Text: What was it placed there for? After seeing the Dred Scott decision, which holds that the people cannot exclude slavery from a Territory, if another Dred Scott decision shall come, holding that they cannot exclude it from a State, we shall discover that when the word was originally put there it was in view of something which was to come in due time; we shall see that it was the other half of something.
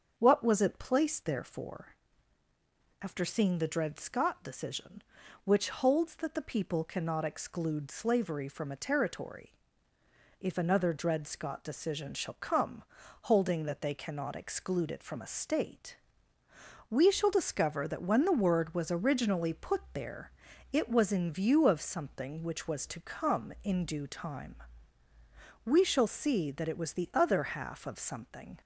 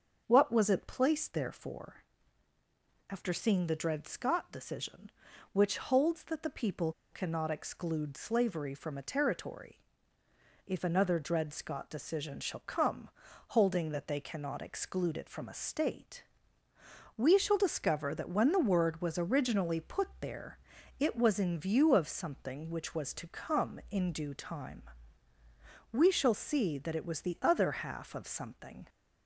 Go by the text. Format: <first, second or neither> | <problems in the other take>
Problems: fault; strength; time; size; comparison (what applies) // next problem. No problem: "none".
first | starts louder than the rest; until 1.2 s; 7 dB; also in the first // pauses between "people" and "cannot"; slight; at 6.9 s; 0.20 s long // pauses between "there" and "it"; at 20.5 s; 0.42 s long; also in the first